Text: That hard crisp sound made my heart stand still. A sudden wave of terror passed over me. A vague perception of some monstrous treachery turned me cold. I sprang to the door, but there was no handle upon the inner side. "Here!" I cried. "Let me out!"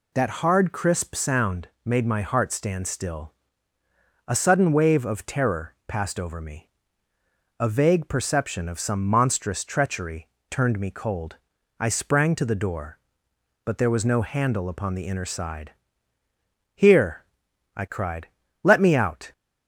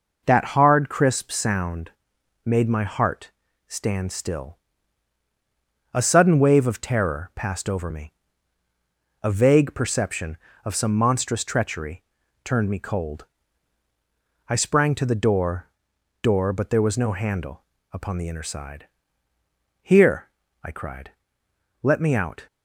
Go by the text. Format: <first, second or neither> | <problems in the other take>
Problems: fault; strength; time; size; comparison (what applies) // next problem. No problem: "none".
first | pauses between "sound" and "made"; noticeable; at 1.8 s; 0.56 s long; slight in the first // pauses between "heart" and "stand"; slight; at 3.3 s; 0.36 s long // pauses between "treachery" and "turned"; at 12.0 s; 0.42 s long; slight in the first // says "door" twice; at 16.2 s // pauses between "handle" and "upon"; slight; at 17.6 s; 0.30 s long